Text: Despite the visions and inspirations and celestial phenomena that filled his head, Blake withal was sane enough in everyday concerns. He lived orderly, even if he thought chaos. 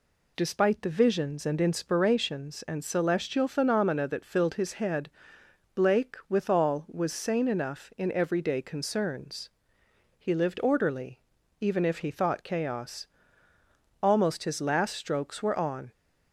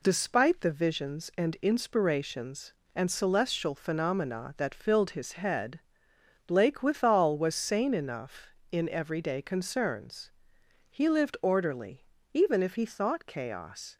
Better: second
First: goes on to say "Almost his last strokes were on"; strong; from 14.0 s on; 1.8 s long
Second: none

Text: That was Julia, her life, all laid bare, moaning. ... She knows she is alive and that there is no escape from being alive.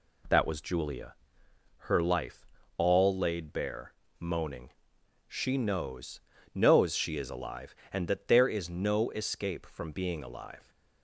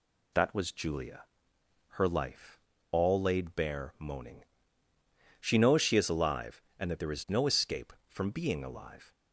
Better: second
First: says "knows" twice; at 6.5 s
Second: none

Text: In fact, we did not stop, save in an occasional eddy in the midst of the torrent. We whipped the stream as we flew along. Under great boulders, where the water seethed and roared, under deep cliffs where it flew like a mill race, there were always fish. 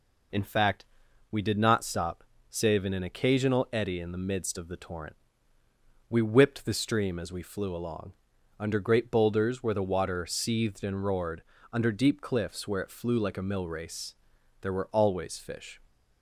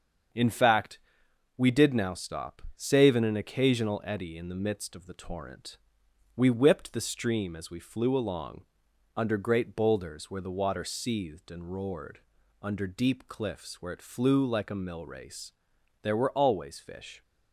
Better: first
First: none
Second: starts louder than the rest; until 1.9 s; 7 dB // says "now" for "not"; at 1.9 s

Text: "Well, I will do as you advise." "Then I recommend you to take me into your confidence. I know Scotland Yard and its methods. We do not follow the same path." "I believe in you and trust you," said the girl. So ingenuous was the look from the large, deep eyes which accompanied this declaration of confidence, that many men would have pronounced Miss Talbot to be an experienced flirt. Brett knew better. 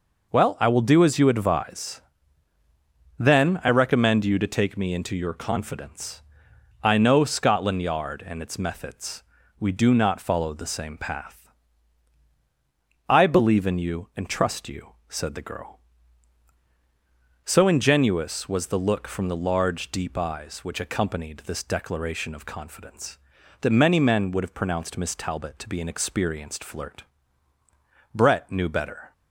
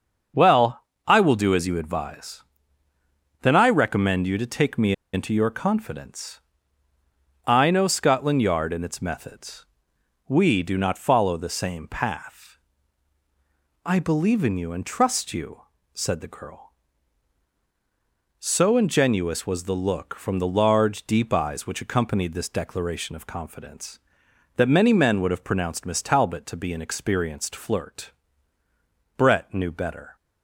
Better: first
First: none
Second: starts louder than the rest; until 1.5 s; 6.5 dB // pauses between "me" and "into"; slight; at 4.9 s; 0.20 s long

